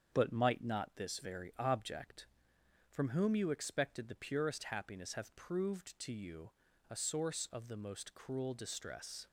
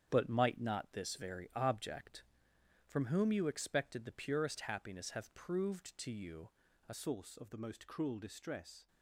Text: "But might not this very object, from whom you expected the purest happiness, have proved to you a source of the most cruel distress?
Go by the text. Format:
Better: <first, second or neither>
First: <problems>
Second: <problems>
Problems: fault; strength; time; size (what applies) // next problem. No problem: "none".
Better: first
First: starts louder than the rest; strong; until 1.1 s; 7 dB // pauses between "you" and "a"; at 6.5 s; 0.38 s long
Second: starts louder than the rest; strong; until 1.1 s; 8.5 dB // pauses between "you" and "a"; at 6.4 s; 0.38 s long // changes voice at "source"; from 6.9 s on; 1.9 s long